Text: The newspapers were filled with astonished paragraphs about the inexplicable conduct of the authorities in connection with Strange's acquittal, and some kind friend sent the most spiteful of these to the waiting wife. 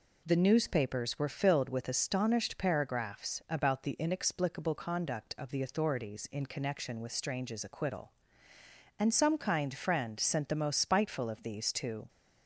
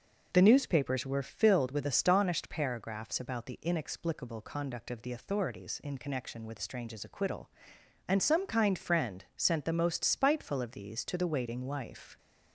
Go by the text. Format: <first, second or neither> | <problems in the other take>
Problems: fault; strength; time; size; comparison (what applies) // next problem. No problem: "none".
second | stops before "the waiting wife"; at 12.0 s